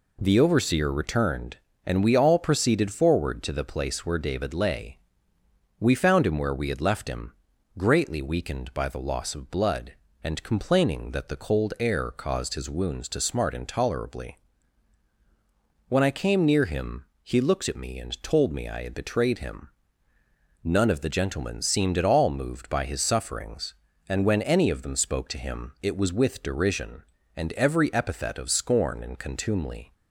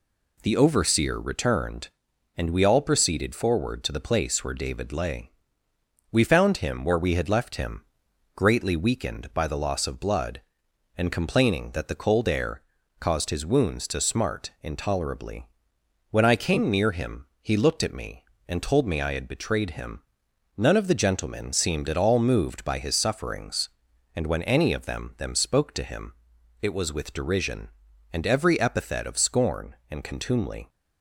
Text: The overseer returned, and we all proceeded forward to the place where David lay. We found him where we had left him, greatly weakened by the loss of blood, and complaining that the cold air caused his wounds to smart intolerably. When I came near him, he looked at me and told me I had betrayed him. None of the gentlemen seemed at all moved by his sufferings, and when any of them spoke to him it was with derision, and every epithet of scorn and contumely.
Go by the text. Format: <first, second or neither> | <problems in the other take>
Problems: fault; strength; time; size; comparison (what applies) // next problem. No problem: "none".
first | pauses between "air" and "caused"; at 12.6 s; 0.40 s long // says "them" twice; at 25.1 s // pauses between "him" and "it"; noticeable; at 26.1 s; 0.48 s long